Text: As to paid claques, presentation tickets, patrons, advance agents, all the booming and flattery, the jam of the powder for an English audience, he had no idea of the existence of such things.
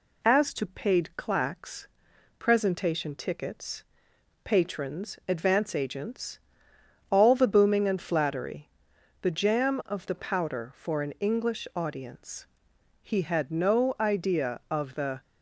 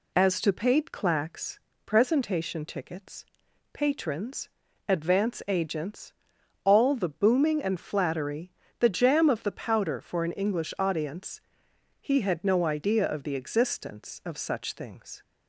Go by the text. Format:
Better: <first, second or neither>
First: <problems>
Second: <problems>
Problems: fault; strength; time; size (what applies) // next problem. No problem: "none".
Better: second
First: stops before "existence of such things"; at 15.2 s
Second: none